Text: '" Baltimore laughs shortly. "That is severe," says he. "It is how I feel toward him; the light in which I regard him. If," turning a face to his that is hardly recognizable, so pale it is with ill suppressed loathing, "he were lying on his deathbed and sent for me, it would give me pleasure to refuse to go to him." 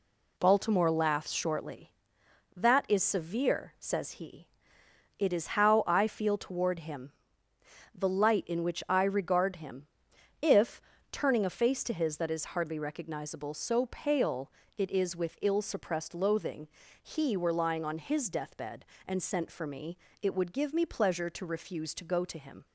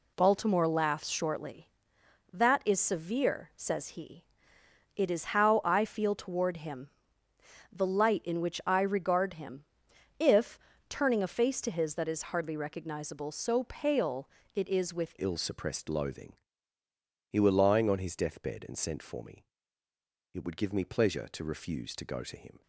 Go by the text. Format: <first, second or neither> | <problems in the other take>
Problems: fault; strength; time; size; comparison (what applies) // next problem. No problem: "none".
first | pauses between "pale" and "it"; slight; at 14.2 s; 0.26 s long; slight in the first // changes voice at "ill"; from 15.1 s on; 7.5 s long